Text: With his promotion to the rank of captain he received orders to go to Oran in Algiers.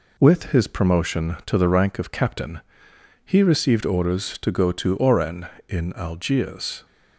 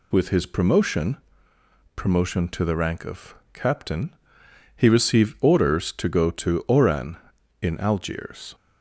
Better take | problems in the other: first | says "promotion" twice; at 1.9 s // pauses between "of" and "captain"; slight; at 3.3 s; 0.20 s long // pauses between "captain" and "he"; noticeable; at 4.1 s; 0.62 s long; noticeable in the first

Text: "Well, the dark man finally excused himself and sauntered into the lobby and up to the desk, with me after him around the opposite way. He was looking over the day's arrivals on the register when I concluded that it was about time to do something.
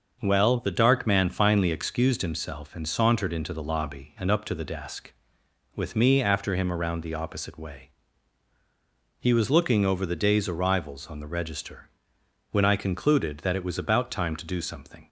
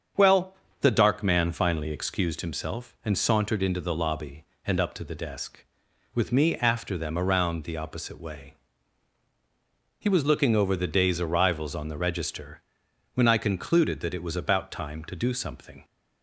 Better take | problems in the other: first | starts louder than the rest; strong; until 1.4 s; 7.5 dB; also in the first // says "them" for "him"; at 6.9 s // pauses between "register" and "when"; noticeable; at 12.6 s; 0.52 s long; noticeable in the first

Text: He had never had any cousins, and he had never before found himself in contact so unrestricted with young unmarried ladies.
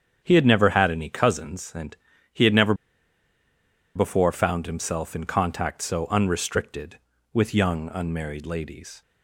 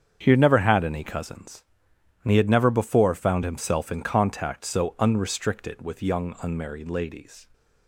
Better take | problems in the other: second | starts louder than the rest; strong; until 1.2 s; 8 dB; strong in the second // pauses between "and" and "he"; slight; at 1.9 s; 0.36 s long // pauses between "never" and "before"; at 2.7 s; 1.2 s long

